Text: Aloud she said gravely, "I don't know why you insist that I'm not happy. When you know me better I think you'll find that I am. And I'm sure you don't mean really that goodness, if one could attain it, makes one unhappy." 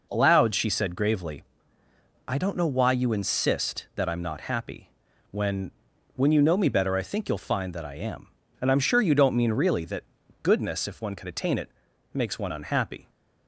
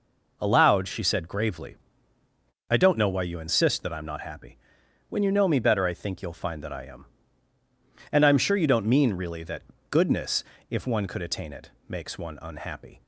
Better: second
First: says "When" twice; at 6.1 s // pauses between "that" and "goodness"; at 10.0 s; 0.38 s long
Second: pauses between "that" and "goodness"; slight; at 9.6 s; 0.26 s long

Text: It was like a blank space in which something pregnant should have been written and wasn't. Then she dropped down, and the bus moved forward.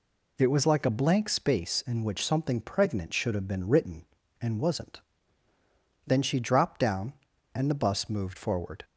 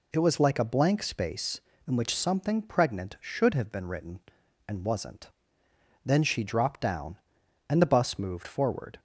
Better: neither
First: none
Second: none

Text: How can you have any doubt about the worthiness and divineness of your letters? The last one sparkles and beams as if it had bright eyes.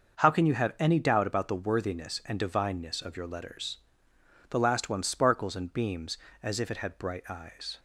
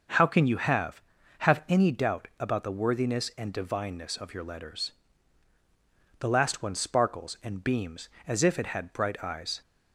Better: first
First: starts louder than the rest; until 1.2 s; 6.5 dB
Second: starts louder than the rest; until 1.5 s; 6.5 dB // says "have" twice; at 1.4 s

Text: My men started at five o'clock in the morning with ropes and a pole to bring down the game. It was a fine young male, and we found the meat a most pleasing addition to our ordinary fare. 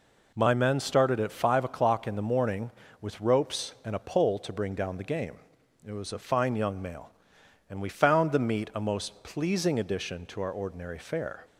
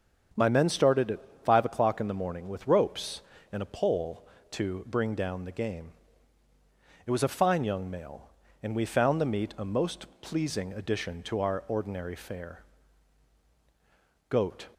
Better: first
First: none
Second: starts louder than the rest; strong; until 1.5 s; 7.5 dB // pauses between "at" and "five"; slight; at 1.2 s; 0.24 s long // pauses between "most" and "pleasing"; slight; at 10.0 s; 0.16 s long // goes on to say "Goat"; slight; from 14.2 s on; 0.40 s long

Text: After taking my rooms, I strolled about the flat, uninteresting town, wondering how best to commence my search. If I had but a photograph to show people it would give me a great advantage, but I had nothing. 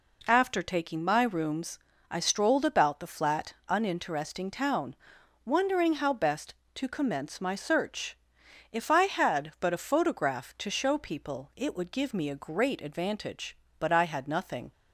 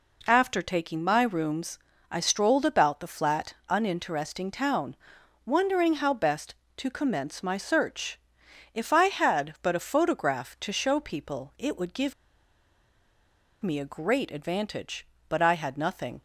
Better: first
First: none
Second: pauses between "give" and "me"; strong; at 12.1 s; 1.4 s long

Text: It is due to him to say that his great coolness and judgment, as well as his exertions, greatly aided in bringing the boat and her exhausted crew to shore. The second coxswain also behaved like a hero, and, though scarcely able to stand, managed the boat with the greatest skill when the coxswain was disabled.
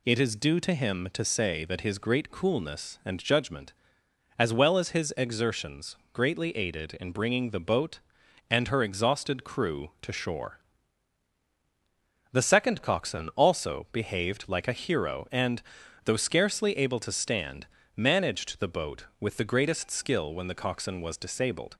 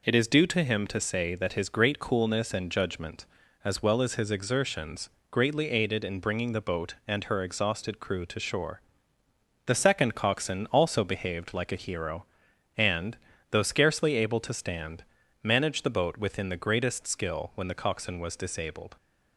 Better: first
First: none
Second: says "within" for "with"; at 16.1 s

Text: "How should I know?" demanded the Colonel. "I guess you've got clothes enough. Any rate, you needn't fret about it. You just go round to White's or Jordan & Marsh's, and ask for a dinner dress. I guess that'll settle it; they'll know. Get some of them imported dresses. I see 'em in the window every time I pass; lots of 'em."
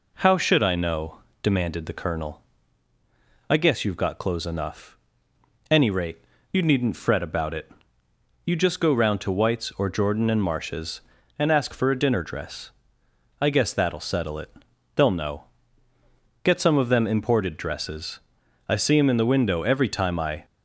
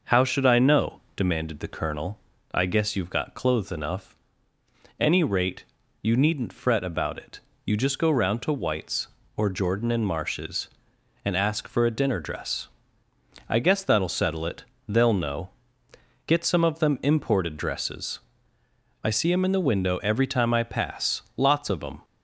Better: second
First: stops before "pass lots of em"; at 20.4 s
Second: none

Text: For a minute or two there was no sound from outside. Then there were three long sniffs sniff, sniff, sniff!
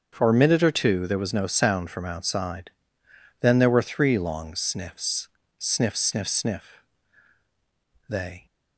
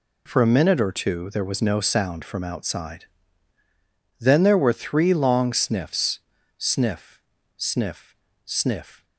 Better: second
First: starts louder than the rest; until 1.1 s; 7 dB // pauses between "sniffs" and "sniff"; slight; at 5.2 s; 0.30 s long // goes on to say "They"; slight; from 8.0 s on; 0.38 s long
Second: pauses between "sniffs" and "sniff"; at 6.1 s; 0.40 s long

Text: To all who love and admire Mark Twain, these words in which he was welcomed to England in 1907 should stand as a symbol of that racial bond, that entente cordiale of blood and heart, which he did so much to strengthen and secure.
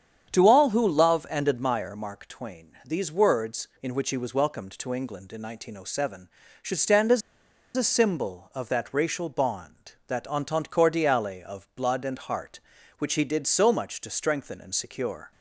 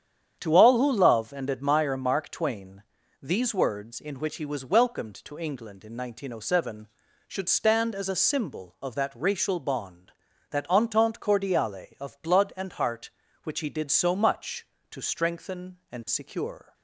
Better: second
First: starts louder than the rest; strong; until 1.3 s; 8 dB // pauses between "as" and "a"; noticeable; at 7.2 s; 0.56 s long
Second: starts louder than the rest; strong; until 1.4 s; 8.5 dB

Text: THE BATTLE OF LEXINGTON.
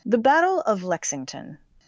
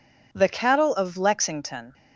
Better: first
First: none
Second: says "Cattle" for "BATTLE"; at 0.4 s

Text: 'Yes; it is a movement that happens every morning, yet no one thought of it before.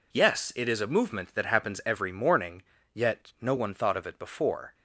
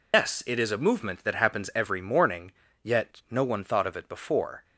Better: first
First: none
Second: loses the start of "Yes"; at 0.1 s; 110 ms

